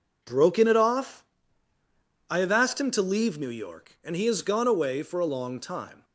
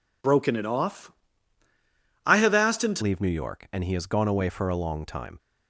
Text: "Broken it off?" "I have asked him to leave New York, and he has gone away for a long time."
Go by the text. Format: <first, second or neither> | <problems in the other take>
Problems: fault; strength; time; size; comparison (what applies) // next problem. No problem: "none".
first | changes voice at "leave"; from 3.0 s on; 2.3 s long